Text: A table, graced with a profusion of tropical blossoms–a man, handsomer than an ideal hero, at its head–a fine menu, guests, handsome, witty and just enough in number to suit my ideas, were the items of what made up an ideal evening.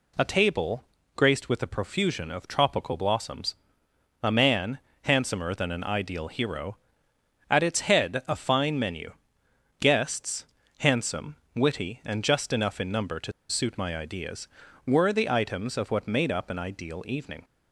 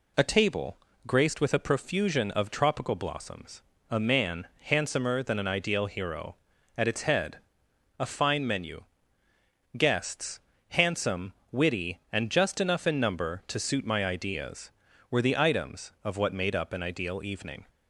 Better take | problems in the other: second | pauses between "to" and "suit"; slight; at 13.3 s; 0.18 s long

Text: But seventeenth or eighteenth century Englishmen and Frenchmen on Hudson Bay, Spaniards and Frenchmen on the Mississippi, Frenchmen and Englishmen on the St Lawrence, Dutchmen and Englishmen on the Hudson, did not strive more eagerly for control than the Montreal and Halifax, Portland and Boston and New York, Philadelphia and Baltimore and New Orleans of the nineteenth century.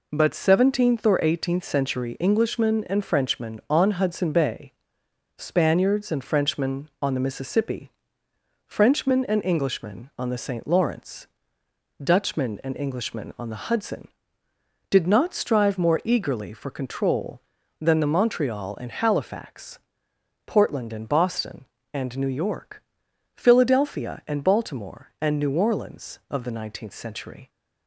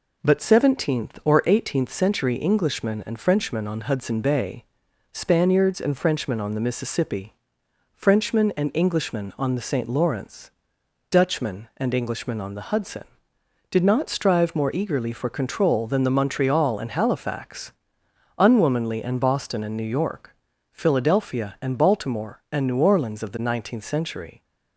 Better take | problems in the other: first | says "Unwomanly" for "Portland"; at 18.3 s

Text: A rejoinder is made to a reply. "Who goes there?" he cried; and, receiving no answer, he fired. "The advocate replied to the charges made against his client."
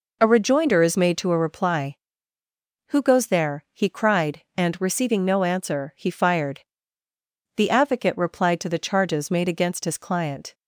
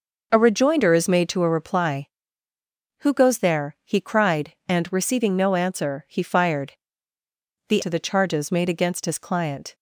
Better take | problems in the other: first | skips "advocate replied"; at 7.8 s

